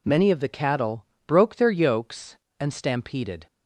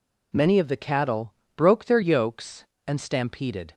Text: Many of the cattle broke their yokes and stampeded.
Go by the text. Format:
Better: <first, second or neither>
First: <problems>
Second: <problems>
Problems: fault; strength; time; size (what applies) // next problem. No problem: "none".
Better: neither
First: pauses between "cattle" and "broke"; slight; at 1.0 s; 0.22 s long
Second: pauses between "cattle" and "broke"; slight; at 1.3 s; 0.24 s long